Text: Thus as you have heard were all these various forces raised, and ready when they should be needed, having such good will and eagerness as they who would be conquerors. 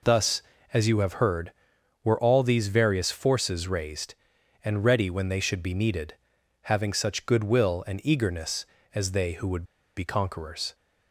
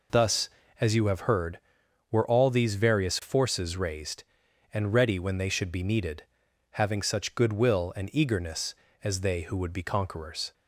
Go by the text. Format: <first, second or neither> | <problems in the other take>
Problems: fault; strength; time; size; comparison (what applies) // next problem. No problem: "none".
second | pauses between "would" and "be"; slight; at 9.6 s; 0.33 s long